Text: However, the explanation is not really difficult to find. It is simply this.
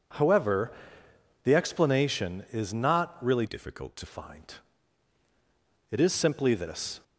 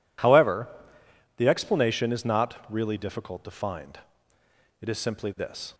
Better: second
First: changes voice from "difficult" to "to"; from 3.4 to 4.0 s; 0.6 s long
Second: none

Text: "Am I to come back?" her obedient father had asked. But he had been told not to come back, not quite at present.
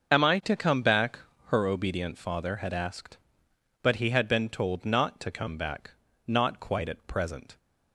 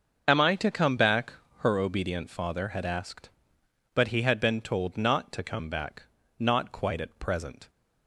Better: neither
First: starts louder than the rest; until 1.1 s; 6.5 dB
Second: starts louder than the rest; until 1.2 s; 6.5 dB

